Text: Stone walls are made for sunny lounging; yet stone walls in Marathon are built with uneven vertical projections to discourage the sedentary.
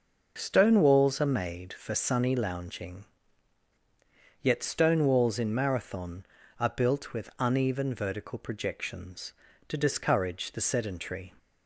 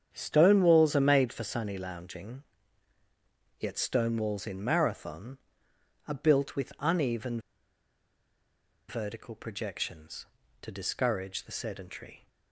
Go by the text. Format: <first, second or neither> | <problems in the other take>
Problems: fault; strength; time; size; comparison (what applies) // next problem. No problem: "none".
first | starts louder than the rest; strong; until 1.1 s; 8.5 dB // pauses between "uneven" and "vertical"; strong; at 7.3 s; 1.4 s long